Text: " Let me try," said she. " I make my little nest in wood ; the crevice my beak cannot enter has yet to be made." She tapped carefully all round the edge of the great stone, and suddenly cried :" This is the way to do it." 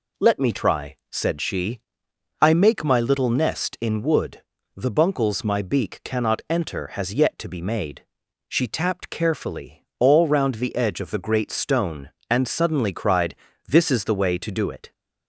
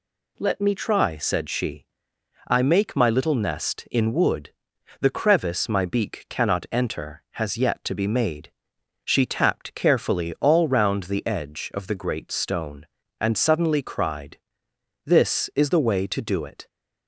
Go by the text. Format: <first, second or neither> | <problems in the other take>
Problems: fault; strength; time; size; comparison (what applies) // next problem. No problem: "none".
second | says "buncles" for "crevice"; at 4.9 s